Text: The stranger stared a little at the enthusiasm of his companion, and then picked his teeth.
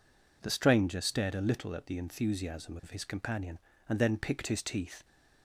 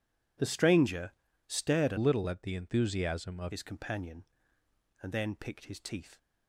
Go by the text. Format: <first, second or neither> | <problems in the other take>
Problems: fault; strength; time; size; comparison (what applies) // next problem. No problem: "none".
first | pauses between "stranger" and "stared"; at 1.1 s; 0.38 s long // changes voice from "little" to "of"; from 1.9 to 3.5 s; 1.6 s long